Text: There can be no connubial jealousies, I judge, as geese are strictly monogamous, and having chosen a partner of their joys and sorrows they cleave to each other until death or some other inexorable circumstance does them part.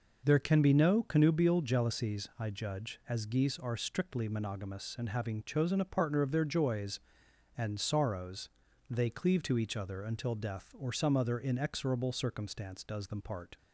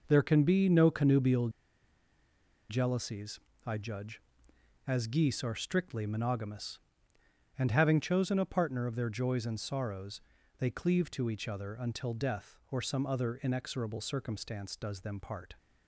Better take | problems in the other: first | pauses between "connubial" and "jealousies"; at 1.4 s; 1.2 s long // pauses between "sorrows" and "they"; at 10.1 s; 0.40 s long; also in the first

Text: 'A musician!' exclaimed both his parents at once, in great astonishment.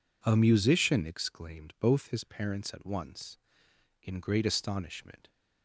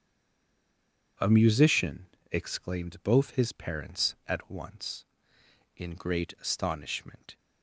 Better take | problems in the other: first | stays silent before the first word; noticeable; until 1.1 s; 1.1 s long // starts louder than the rest; strong; until 2.4 s; 8 dB

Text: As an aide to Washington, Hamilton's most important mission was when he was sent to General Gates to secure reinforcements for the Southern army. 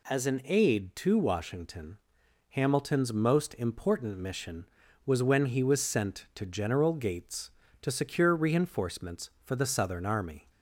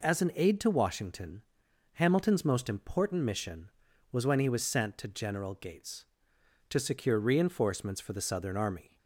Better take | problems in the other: neither | none

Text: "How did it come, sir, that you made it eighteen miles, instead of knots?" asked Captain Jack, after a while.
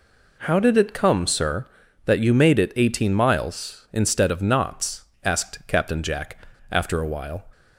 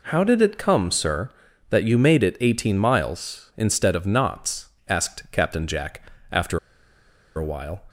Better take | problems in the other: first | pauses between "after" and "a"; noticeable; at 6.5 s; 0.77 s long

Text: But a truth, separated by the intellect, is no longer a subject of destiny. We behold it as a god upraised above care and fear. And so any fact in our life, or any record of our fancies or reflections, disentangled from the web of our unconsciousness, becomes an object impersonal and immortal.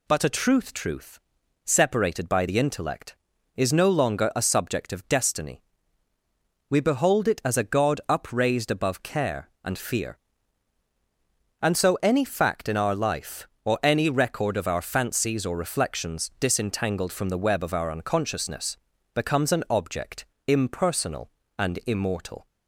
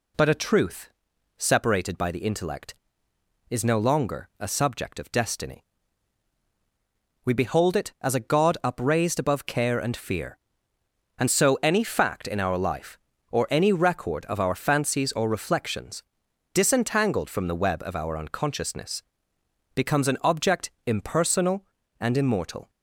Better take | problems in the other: second | says "truth" twice; at 0.7 s // pauses between "object" and "impersonal"; slight; at 20.2 s; 0.22 s long; slight in the second

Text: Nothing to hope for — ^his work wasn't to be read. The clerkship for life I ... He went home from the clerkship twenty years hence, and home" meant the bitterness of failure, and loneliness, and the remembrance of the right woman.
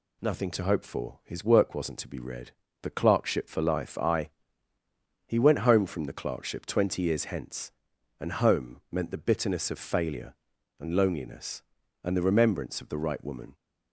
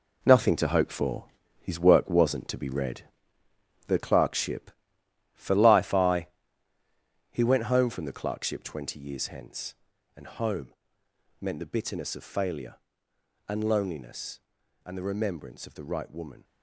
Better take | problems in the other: first | gets quieter; strong; throughout; 9.5 dB // pauses between "home" and "meant"; noticeable; at 10.7 s; 0.66 s long

